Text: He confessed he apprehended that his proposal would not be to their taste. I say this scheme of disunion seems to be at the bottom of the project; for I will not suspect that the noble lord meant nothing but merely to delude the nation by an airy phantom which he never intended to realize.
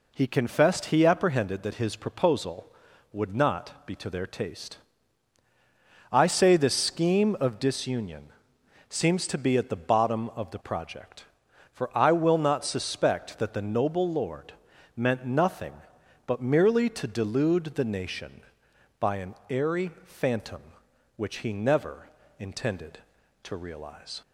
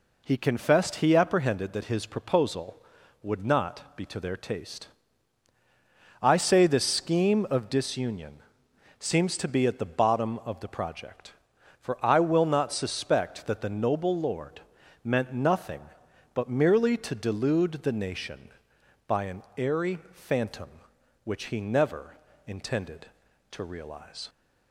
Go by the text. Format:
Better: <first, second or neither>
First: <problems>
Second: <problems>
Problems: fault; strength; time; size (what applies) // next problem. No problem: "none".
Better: neither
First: pauses between "disunion" and "seems"; noticeable; at 8.2 s; 0.60 s long // pauses between "lord" and "meant"; at 14.5 s; 0.42 s long // pauses between "never" and "intended"; slight; at 22.0 s; 0.32 s long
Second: pauses between "disunion" and "seems"; noticeable; at 8.3 s; 0.60 s long // pauses between "lord" and "meant"; at 14.6 s; 0.42 s long // pauses between "never" and "intended"; slight; at 22.1 s; 0.32 s long